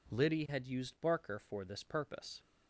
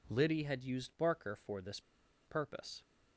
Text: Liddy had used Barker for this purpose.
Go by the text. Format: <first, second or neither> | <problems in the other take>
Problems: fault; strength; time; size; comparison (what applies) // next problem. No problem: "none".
first | pauses between "this" and "purpose"; noticeable; at 1.7 s; 0.47 s long